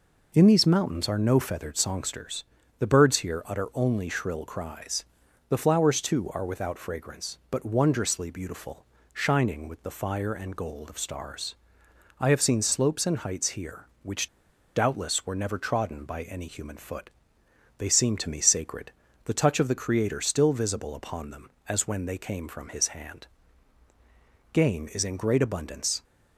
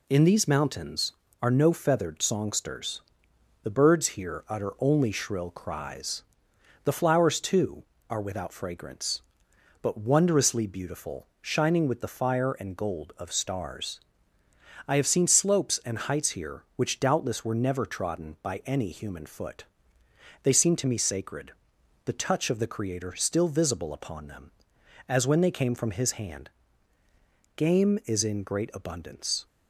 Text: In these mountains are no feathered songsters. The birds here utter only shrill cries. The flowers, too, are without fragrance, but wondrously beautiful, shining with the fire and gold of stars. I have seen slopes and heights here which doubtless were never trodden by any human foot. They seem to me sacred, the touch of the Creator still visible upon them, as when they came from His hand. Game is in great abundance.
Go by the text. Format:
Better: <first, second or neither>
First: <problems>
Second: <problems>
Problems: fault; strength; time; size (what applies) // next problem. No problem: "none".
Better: second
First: pauses between "which" and "doubtless"; noticeable; at 14.2 s; 0.49 s long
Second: none